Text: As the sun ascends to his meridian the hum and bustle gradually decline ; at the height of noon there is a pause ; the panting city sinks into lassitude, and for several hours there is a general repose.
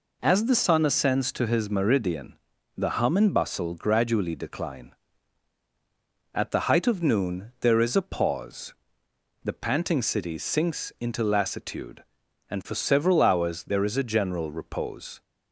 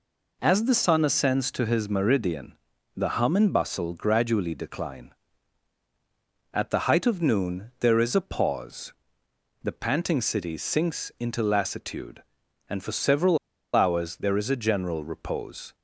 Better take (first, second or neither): first